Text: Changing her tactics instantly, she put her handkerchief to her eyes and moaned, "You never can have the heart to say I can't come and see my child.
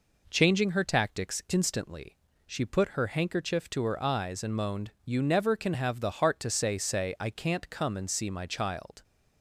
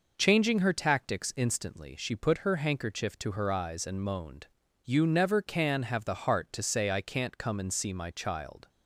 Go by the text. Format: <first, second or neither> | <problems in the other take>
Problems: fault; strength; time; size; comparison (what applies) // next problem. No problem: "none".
second | says "say" twice; at 6.7 s